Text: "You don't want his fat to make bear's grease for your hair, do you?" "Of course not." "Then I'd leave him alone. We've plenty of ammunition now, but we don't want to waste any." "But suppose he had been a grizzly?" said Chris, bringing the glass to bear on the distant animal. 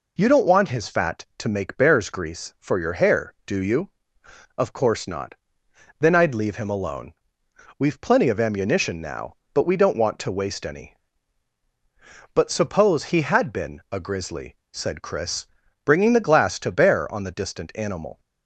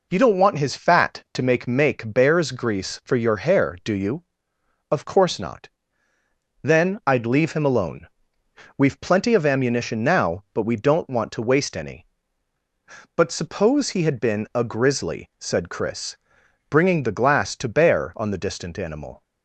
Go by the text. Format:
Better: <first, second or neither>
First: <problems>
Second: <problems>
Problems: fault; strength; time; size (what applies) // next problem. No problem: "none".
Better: first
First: none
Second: says "make" twice; at 1.6 s